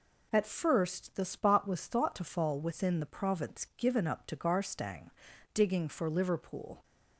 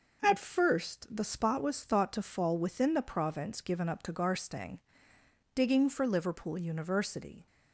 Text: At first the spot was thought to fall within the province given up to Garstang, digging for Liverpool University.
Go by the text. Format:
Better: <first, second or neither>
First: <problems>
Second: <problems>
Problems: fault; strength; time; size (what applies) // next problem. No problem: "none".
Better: second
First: stops before "University"; at 6.8 s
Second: none